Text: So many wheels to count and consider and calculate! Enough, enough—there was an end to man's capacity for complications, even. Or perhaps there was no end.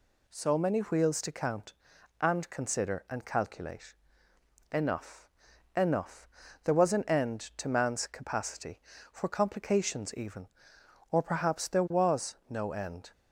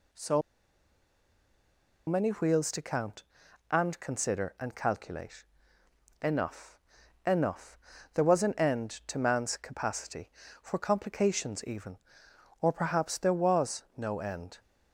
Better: first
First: none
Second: pauses between "So" and "many"; strong; at 0.4 s; 1.6 s long

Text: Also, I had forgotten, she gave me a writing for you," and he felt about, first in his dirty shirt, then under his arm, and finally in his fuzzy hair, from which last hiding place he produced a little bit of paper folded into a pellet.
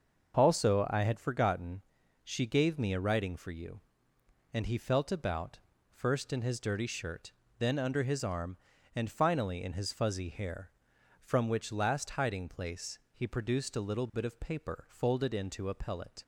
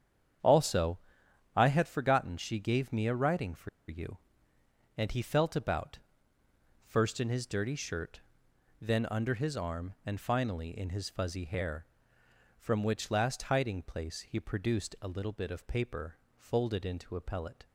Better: first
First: starts louder than the rest; until 1.4 s; 6.5 dB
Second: starts louder than the rest; strong; until 2.0 s; 8.5 dB // pauses between "for" and "you"; slight; at 3.6 s; 0.20 s long // pauses between "paper" and "folded"; slight; at 16.1 s; 0.22 s long

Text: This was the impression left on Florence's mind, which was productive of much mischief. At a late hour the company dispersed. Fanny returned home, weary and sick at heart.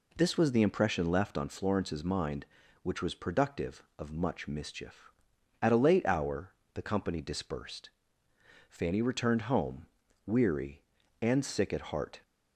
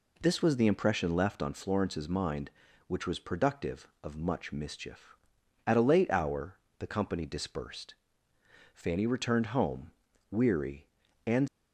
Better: first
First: pauses between "hour" and "the"; slight; at 6.5 s; 0.24 s long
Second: pauses between "hour" and "the"; slight; at 6.5 s; 0.24 s long // stops before "sick at heart"; at 11.4 s

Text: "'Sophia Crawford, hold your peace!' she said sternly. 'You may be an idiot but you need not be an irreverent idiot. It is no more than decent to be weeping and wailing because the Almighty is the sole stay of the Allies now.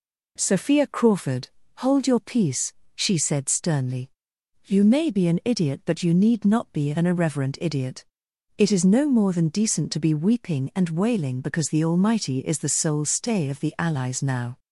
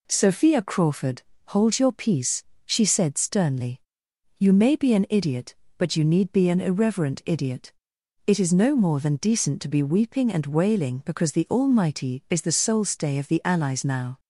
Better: first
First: none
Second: skips "not"; at 6.3 s

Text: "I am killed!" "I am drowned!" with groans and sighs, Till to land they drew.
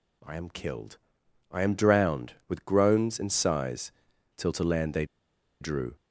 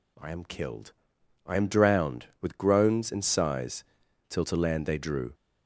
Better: second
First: pauses between "they" and "drew"; noticeable; at 5.0 s; 0.55 s long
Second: none

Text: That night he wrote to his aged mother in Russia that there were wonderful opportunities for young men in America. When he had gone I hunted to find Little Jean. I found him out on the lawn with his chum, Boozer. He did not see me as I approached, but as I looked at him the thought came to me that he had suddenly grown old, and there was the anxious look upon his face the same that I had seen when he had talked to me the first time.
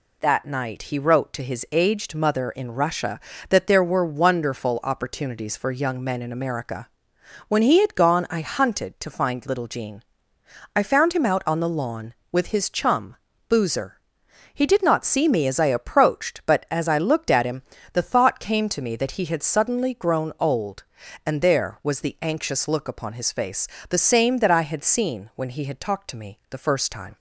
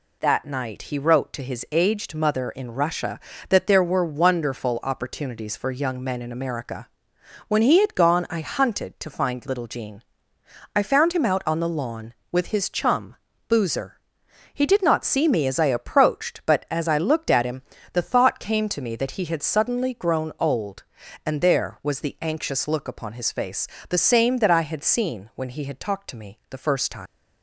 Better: first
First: pauses between "him" and "the"; slight; at 17.6 s; 0.30 s long // pauses between "face" and "the"; slight; at 23.6 s; 0.22 s long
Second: pauses between "him" and "the"; slight; at 17.6 s; 0.30 s long // pauses between "face" and "the"; slight; at 23.6 s; 0.22 s long // leaves "time" unfinished; at 27.0 s; 95 ms

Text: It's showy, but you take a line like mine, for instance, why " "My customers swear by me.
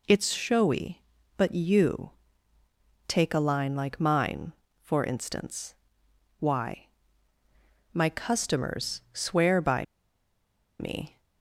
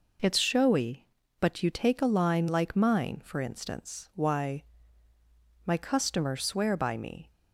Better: second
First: pauses between "you" and "take"; noticeable; at 2.1 s; 0.96 s long // pauses between "by" and "me"; noticeable; at 9.8 s; 0.94 s long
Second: none

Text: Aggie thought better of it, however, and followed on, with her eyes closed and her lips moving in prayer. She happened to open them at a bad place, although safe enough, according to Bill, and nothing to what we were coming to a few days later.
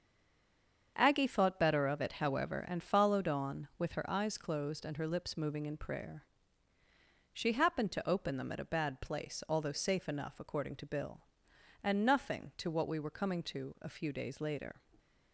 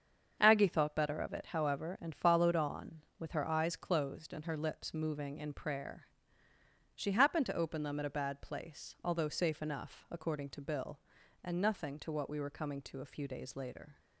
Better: second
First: stays silent before the first word; slight; until 0.9 s; 0.9 s long // starts louder than the rest; strong; until 1.9 s; 7 dB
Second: starts louder than the rest; until 1.4 s; 7 dB

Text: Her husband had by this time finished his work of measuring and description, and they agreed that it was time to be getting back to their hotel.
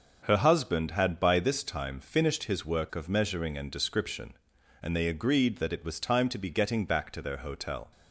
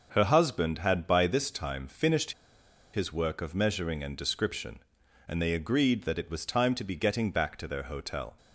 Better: first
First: none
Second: pauses between "finished" and "his"; noticeable; at 2.3 s; 0.62 s long

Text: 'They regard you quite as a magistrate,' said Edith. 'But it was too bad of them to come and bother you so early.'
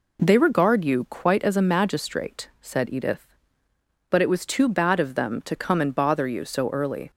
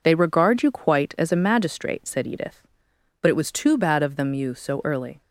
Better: first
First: none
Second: skips "to come and bother"; at 4.3 s

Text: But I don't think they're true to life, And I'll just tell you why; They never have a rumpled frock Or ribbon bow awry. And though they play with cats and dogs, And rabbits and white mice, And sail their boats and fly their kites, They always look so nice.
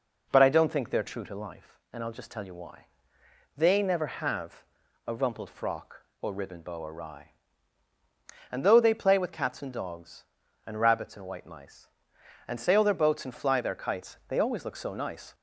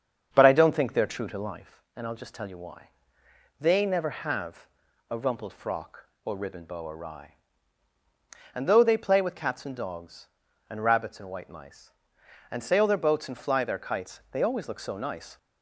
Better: first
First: pauses between "have" and "a"; at 4.6 s; 0.42 s long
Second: starts louder than the rest; strong; until 1.9 s; 7 dB // pauses between "have" and "a"; at 4.6 s; 0.42 s long

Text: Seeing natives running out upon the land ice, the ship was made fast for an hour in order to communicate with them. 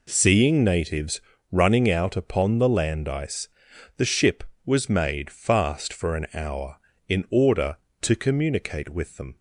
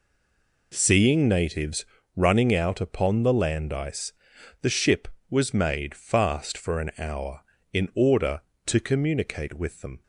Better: first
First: pauses between "natives" and "running"; slight; at 1.2 s; 0.32 s long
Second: stays silent before the first word; slight; until 0.7 s; 0.7 s long // pauses between "natives" and "running"; slight; at 1.8 s; 0.32 s long

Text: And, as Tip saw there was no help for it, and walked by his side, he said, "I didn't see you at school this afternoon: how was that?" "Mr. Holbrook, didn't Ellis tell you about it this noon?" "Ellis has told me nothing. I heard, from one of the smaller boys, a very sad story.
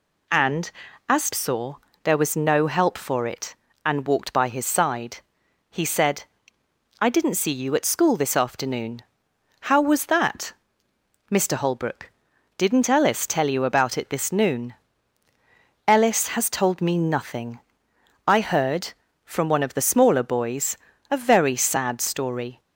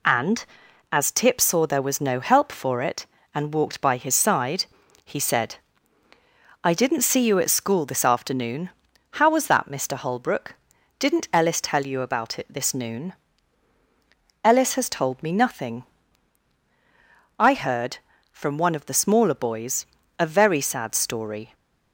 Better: second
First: skips "Tip"; at 1.3 s // pauses between "saw" and "there"; slight; at 1.7 s; 0.28 s long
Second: none

